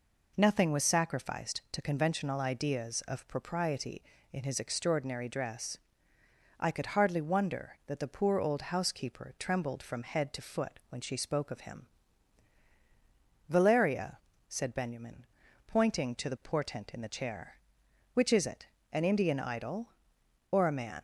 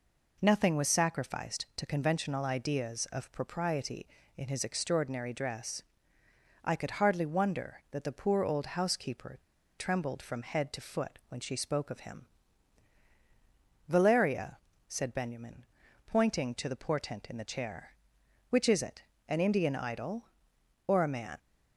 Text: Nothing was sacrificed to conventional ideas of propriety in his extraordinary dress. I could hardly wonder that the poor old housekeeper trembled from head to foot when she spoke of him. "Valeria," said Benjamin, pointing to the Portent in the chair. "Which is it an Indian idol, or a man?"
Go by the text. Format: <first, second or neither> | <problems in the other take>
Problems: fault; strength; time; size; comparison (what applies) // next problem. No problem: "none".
first | pauses between "housekeeper" and "trembled"; at 9.3 s; 0.39 s long // pauses between "it" and "an"; slight; at 19.0 s; 0.24 s long; slight in the first